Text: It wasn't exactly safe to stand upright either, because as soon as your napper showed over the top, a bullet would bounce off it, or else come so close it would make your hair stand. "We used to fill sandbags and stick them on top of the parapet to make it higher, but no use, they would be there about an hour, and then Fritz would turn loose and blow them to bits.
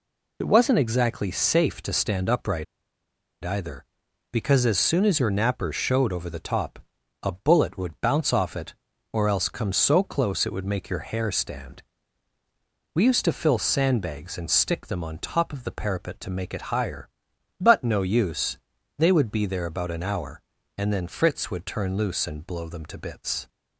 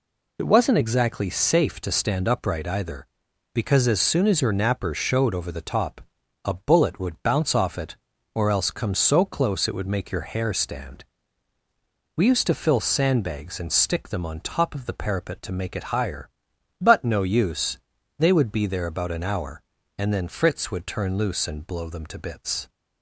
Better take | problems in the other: second | pauses between "upright" and "either"; noticeable; at 2.6 s; 0.79 s long

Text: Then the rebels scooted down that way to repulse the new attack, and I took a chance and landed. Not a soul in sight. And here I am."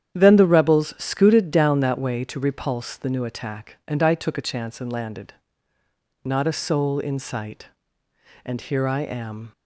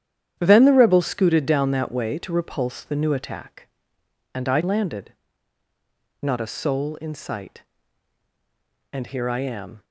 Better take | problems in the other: first | starts louder than the rest; strong; until 1.4 s; 10 dB; strong in the first // skips "took a chance and"; at 4.6 s

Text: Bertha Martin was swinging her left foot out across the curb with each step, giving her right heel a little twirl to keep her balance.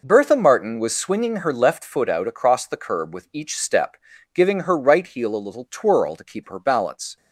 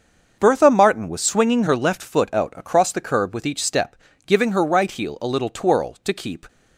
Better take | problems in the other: first | starts louder than the rest; until 1.3 s; 6.5 dB // stops before "her balance"; at 6.4 s

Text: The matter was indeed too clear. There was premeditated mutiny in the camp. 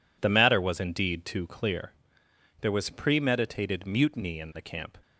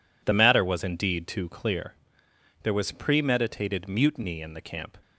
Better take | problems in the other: neither | none

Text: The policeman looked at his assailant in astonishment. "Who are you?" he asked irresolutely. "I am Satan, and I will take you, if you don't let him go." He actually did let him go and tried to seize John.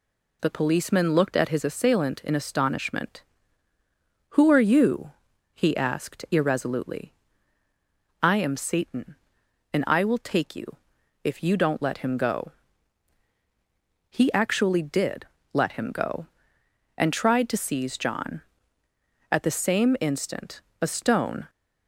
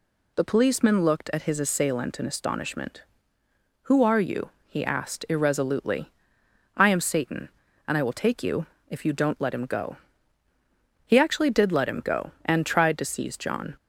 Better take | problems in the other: second | pauses between "did" and "let"; slight; at 15.2 s; 0.26 s long // goes on to say "At the same instant a stone"; strong; from 19.2 s on; 2.2 s long

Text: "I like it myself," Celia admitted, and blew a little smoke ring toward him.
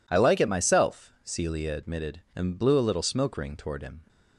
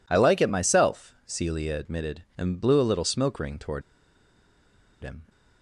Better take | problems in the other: first | pauses between "toward" and "him"; at 3.8 s; 1.2 s long

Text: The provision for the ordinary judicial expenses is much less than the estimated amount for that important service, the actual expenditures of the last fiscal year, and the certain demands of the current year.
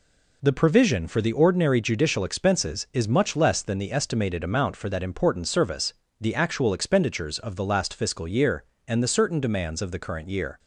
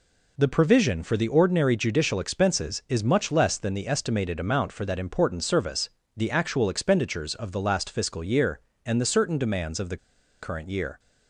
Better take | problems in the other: first | pauses between "the" and "current"; at 9.9 s; 0.45 s long

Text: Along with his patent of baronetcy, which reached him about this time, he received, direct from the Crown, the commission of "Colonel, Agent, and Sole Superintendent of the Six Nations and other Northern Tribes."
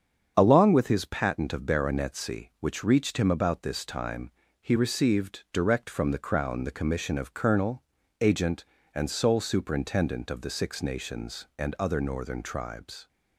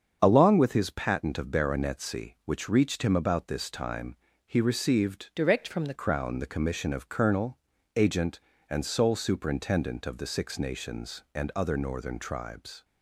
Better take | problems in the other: first | starts louder than the rest; strong; until 1.2 s; 7 dB; strong in the first // changes voice from "direct" to "the"; from 5.3 to 5.9 s; 0.6 s long

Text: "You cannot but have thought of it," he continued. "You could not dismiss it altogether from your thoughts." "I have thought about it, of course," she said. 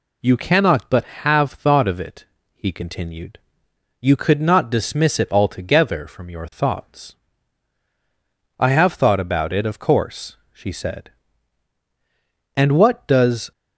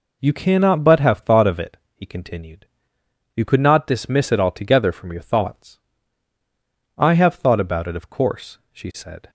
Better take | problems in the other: second | goes on to say "And what does"; noticeable; from 12.5 s on; 0.96 s long

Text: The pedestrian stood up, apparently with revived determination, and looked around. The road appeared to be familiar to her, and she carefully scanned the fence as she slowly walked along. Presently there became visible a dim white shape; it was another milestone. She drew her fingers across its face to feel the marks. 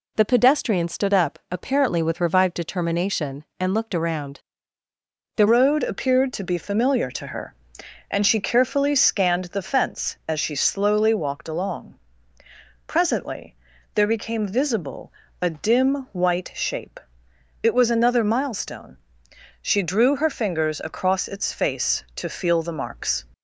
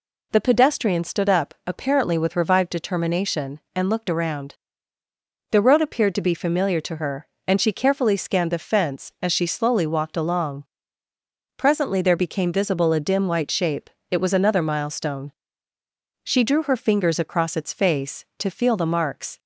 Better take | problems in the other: second | changes voice at "road"; from 5.4 s on; 17.8 s long // pauses between "Presently" and "there"; at 13.5 s; 0.40 s long // pauses between "visible" and "a"; slight; at 15.1 s; 0.26 s long

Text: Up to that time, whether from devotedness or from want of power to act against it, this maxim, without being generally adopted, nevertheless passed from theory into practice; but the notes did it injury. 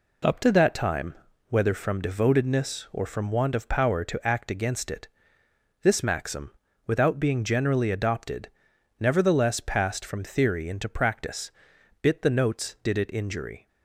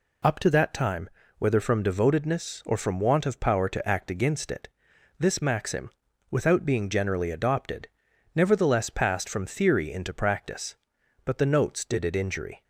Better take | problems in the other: second | says "bit" for "but"; at 12.0 s

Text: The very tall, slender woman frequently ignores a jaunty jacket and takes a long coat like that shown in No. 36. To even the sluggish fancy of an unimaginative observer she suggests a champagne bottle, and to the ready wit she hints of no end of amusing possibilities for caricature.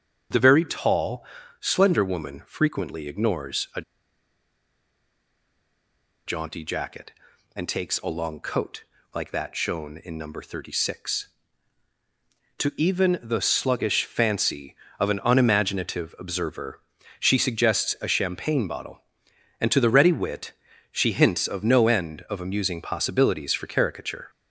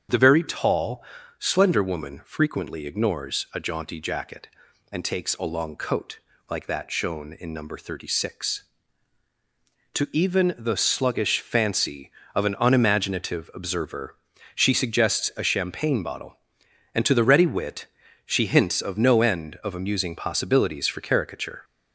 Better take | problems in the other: second | starts louder than the rest; strong; until 1.6 s; 8 dB; strong in the second // pauses between "a" and "jaunty"; strong; at 3.8 s; 2.4 s long // pauses between "coat" and "like"; slight; at 8.8 s; 0.32 s long; slight in the second // pauses between "observer" and "she"; at 16.7 s; 0.40 s long; also in the second // pauses between "wit" and "she"; at 20.4 s; 0.40 s long; also in the second

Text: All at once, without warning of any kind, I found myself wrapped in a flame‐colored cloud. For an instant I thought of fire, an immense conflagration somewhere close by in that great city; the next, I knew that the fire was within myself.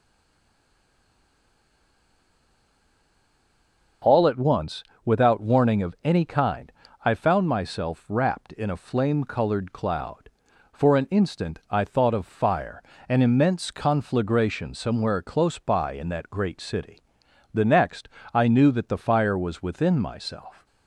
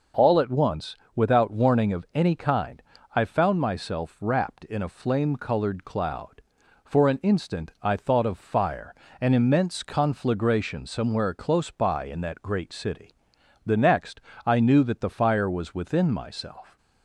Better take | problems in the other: second | stays silent before the first word; strong; until 4.0 s; 4.0 s long

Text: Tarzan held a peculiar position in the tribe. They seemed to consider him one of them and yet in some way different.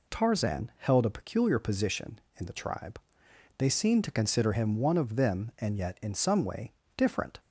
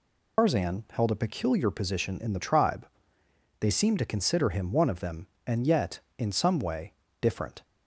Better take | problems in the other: first | loses the start of "Tarzan"; at 0.3 s; 125 ms // pauses between "way" and "different"; slight; at 6.9 s; 0.28 s long; slight in the first

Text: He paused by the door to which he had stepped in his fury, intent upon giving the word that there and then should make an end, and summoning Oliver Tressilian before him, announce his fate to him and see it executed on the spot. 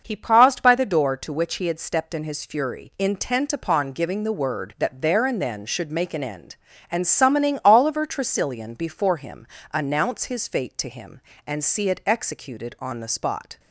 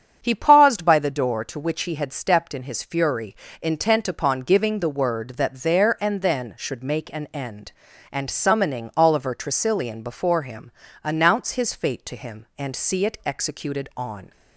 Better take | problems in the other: first | starts louder than the rest; strong; until 1.2 s; 7.5 dB // stops before "the spot"; at 14.3 s

